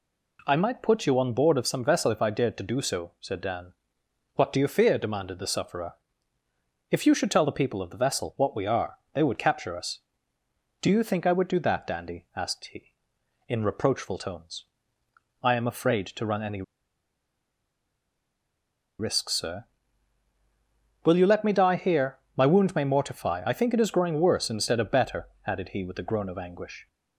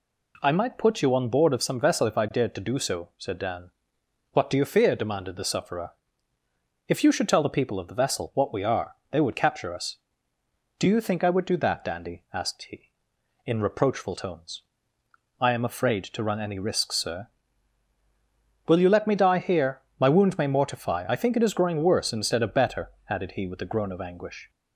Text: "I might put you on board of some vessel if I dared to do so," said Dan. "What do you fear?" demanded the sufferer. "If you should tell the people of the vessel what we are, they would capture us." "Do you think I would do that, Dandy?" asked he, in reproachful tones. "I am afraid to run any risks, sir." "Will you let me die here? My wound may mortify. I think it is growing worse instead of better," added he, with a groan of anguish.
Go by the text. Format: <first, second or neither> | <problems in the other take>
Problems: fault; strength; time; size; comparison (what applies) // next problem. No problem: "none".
second | pauses between "any" and "risks"; strong; at 16.6 s; 2.3 s long